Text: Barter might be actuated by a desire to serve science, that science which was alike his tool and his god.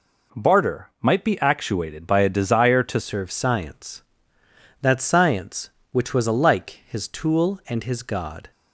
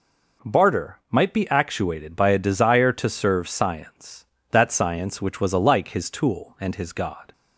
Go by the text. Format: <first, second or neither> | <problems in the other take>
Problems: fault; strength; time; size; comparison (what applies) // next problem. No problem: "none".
second | changes voice at "serve"; from 3.0 s on; 5.5 s long